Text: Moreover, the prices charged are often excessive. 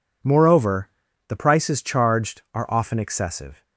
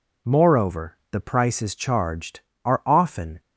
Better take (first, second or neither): first